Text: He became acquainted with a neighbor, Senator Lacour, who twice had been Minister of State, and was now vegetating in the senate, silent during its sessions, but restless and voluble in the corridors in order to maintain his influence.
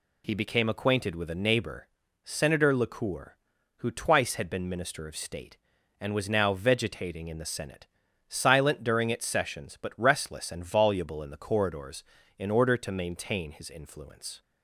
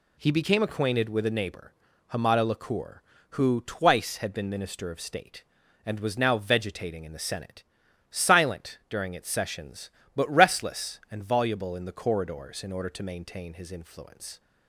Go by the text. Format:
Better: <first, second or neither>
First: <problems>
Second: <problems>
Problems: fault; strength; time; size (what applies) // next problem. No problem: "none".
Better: first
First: none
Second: says "Hamada" for "Senator"; at 2.1 s